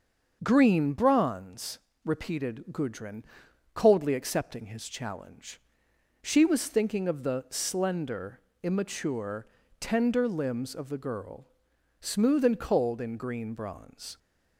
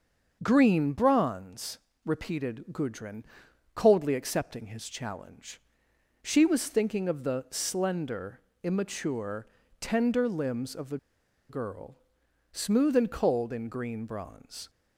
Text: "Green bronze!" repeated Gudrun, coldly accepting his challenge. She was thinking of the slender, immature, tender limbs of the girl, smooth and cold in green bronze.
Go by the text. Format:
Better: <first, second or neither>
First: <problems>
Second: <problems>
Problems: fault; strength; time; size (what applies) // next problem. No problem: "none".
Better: first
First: starts louder than the rest; until 1.4 s; 6.5 dB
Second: starts louder than the rest; until 1.4 s; 6.5 dB // pauses between "the" and "girl"; noticeable; at 10.9 s; 0.51 s long